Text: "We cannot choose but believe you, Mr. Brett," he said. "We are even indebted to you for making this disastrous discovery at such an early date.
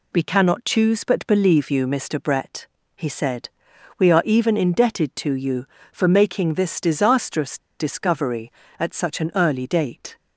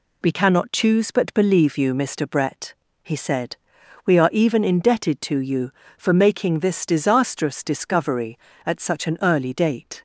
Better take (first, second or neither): second